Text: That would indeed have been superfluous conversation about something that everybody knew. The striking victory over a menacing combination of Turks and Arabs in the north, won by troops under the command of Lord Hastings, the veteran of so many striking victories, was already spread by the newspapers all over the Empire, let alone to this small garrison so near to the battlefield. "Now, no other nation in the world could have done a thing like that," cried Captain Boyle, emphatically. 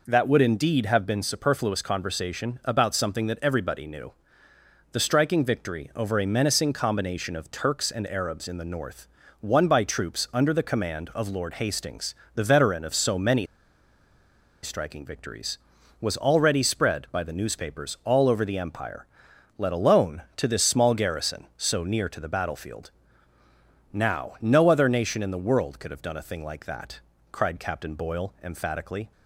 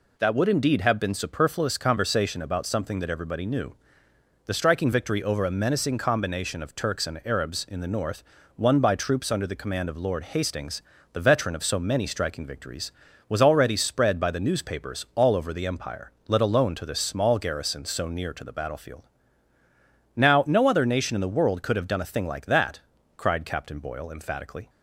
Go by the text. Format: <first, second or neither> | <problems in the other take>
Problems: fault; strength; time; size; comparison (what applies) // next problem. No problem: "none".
second | pauses between "many" and "striking"; at 13.4 s; 1.1 s long